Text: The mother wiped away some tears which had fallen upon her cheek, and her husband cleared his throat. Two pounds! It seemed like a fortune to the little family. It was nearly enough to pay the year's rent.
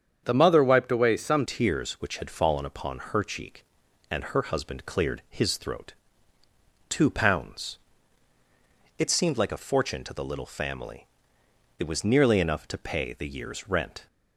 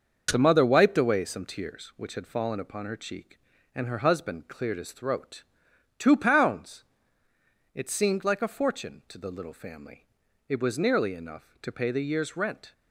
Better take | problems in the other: second | starts louder than the rest; strong; until 1.2 s; 7.5 dB; noticeable in the second // changes voice at "tears"; from 1.4 s on; 12.6 s long

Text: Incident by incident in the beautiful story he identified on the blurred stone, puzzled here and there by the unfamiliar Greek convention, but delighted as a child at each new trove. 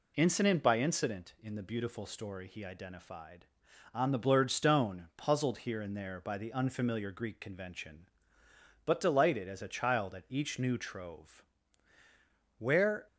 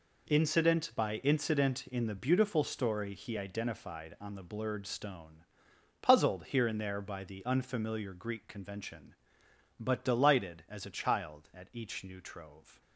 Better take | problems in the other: second | goes on to say "Where"; slight; from 12.5 s on; 0.48 s long

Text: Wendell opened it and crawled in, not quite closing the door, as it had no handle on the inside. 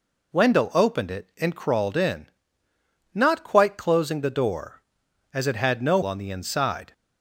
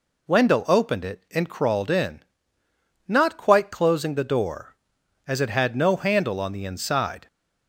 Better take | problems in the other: second | skips "handle"; at 6.0 s

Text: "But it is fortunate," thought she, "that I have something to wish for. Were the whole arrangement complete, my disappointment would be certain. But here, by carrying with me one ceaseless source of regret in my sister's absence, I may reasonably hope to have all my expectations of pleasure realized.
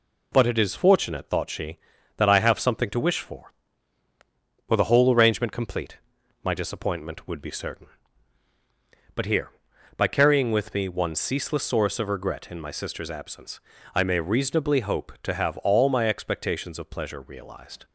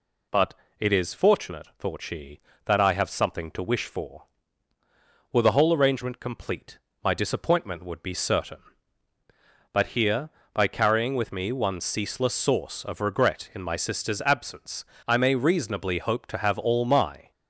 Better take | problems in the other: first | pauses between "But" and "it"; slight; at 0.5 s; 0.24 s long // stops before "expectations of pleasure realized"; at 17.3 s

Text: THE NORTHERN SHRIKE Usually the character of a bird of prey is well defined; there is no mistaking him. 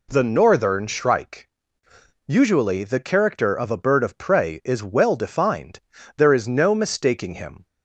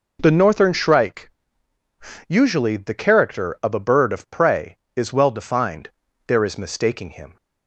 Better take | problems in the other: first | pauses between "SHRIKE" and "Usually"; noticeable; at 1.3 s; 0.98 s long; noticeable in the first // skips "no"; at 6.5 s

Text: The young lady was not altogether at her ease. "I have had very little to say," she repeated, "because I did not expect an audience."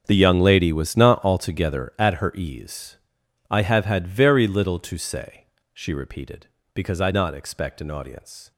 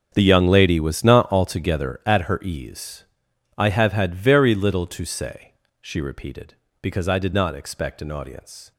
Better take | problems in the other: second | starts louder than the rest; until 1.0 s; 7 dB; also in the second // skips "did"; at 7.1 s

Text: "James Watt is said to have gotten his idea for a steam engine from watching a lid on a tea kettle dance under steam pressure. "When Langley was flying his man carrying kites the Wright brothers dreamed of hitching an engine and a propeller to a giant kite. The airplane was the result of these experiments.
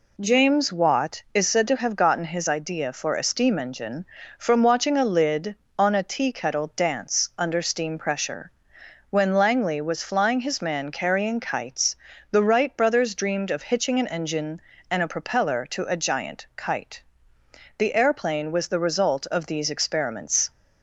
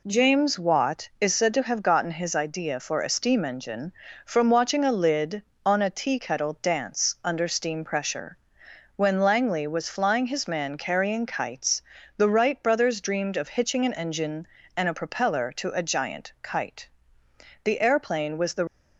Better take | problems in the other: first | pauses between "kites" and "the"; slight; at 11.8 s; 0.34 s long; slight in the first // stops before "result of these experiments"; at 18.6 s

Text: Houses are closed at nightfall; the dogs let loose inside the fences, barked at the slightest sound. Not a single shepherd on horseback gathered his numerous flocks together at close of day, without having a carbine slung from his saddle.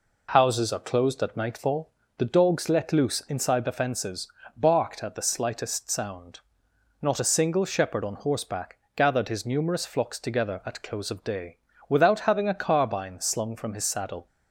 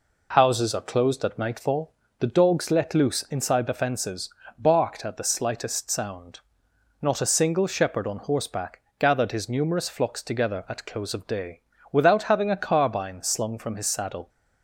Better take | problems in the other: neither | pauses between "horseback" and "gathered"; slight; the same in both

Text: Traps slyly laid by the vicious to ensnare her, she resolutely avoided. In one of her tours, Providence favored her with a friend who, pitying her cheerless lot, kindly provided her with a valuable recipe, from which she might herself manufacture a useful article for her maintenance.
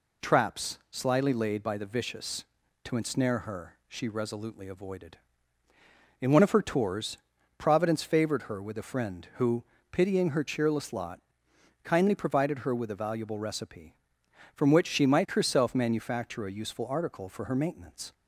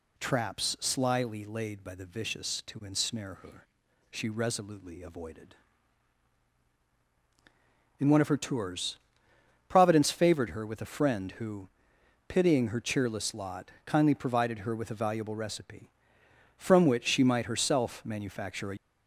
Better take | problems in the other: first | stops before "useful article for her maintenance"; at 18.7 s

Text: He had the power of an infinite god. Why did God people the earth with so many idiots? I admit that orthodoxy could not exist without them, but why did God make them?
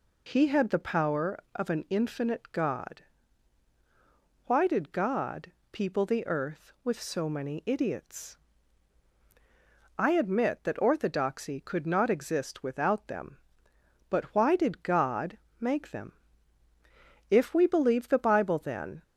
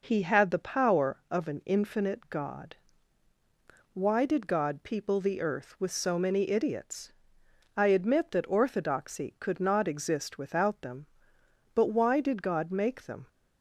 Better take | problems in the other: second | pauses between "God" and "people"; slight; at 5.5 s; 0.18 s long // pauses between "God" and "make"; slight; at 15.3 s; 0.22 s long // goes on to say "If we believe the bible then"; strong; from 17.3 s on; 1.7 s long

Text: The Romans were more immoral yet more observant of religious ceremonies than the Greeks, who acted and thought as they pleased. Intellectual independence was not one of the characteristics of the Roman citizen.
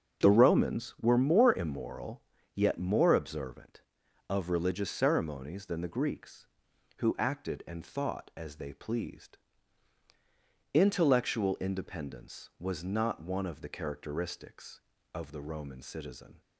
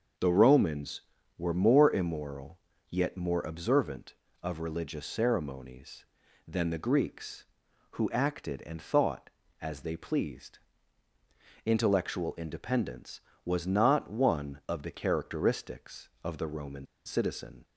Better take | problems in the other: first | starts louder than the rest; until 1.5 s; 6.5 dB; strong in the first // pauses between "immoral" and "yet"; slight; at 2.5 s; 0.30 s long; slight in the first // pauses between "Roman" and "citizen"; slight; at 16.8 s; 0.19 s long

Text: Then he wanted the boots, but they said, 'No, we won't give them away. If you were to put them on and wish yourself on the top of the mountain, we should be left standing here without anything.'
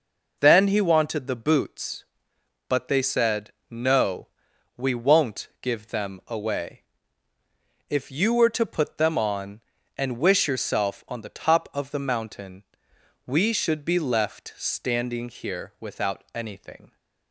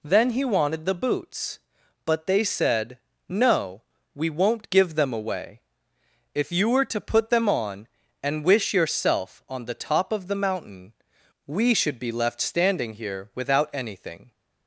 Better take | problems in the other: neither | none

